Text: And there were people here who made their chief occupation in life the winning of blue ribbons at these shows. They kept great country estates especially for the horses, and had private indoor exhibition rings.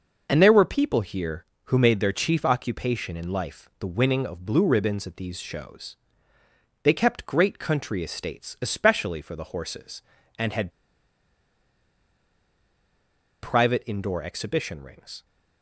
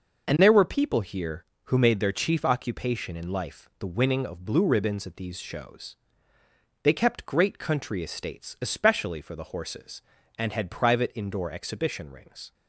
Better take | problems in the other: second | pauses between "had" and "private"; strong; at 10.6 s; 2.7 s long

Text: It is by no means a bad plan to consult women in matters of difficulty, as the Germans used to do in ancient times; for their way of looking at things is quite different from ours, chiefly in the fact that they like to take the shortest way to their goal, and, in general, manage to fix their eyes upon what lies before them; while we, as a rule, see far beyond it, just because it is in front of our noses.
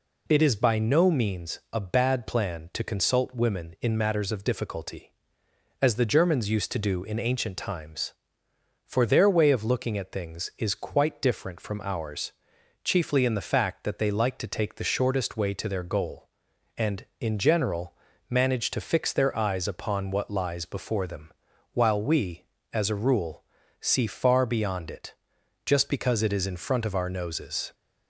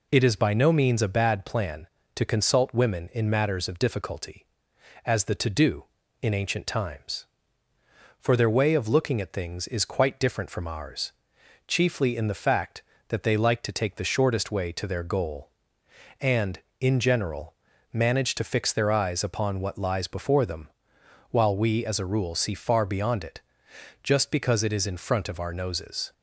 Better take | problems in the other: first | skips "Germans used"; at 5.3 s

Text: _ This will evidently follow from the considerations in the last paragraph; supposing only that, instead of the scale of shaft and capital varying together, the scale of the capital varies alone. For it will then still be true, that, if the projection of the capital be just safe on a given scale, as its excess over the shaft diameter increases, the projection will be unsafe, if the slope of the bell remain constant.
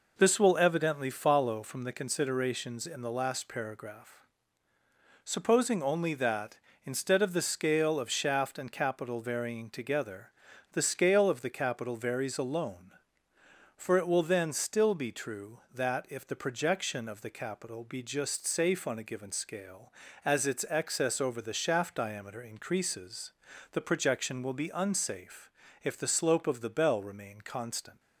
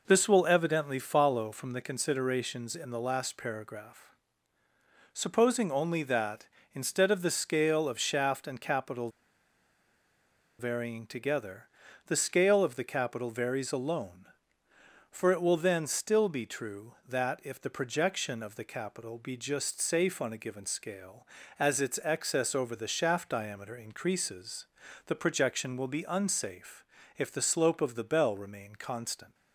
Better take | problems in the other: first | pauses between "capital" and "varying"; strong; at 9.1 s; 1.4 s long

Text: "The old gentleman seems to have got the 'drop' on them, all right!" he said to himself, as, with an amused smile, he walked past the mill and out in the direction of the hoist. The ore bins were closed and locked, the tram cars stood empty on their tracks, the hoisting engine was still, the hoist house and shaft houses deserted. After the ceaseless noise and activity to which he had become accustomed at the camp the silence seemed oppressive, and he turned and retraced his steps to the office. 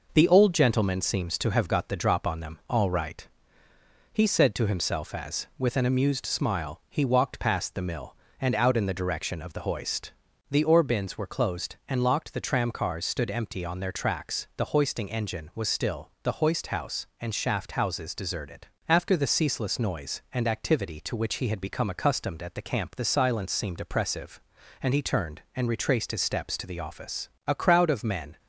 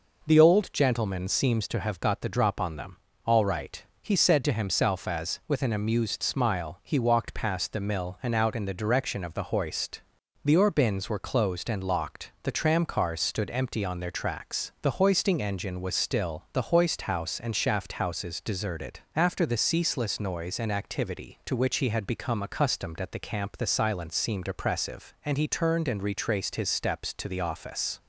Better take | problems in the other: second | goes on to say "A crowd of men"; noticeable; from 27.4 s on; 0.92 s long

